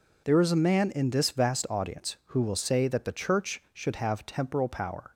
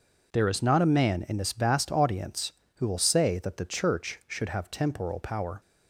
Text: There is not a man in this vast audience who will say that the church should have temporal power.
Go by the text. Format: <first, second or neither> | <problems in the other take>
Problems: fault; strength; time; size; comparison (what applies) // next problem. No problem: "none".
second | skips "not"; at 0.5 s